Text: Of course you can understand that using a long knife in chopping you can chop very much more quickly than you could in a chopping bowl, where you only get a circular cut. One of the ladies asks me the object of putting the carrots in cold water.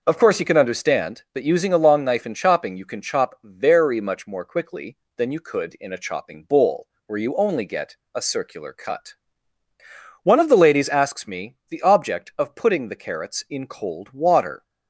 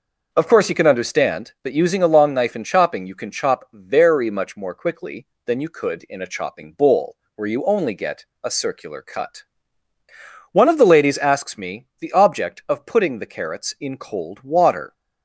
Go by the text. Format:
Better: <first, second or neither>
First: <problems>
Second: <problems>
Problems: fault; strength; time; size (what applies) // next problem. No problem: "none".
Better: neither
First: pauses between "get" and "a"; slight; at 7.9 s; 0.16 s long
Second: pauses between "get" and "a"; slight; at 8.2 s; 0.16 s long